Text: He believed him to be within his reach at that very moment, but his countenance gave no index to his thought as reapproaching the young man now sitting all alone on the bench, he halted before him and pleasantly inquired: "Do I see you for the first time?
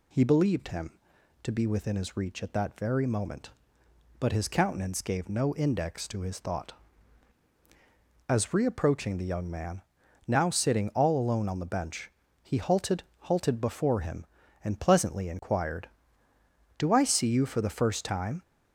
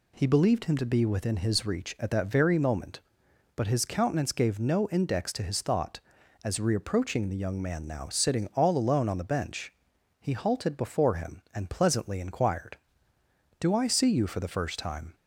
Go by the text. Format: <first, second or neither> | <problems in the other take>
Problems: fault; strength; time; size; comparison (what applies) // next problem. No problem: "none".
second | pauses between "man" and "now"; noticeable; at 9.8 s; 0.46 s long // says "halted" twice; at 13.2 s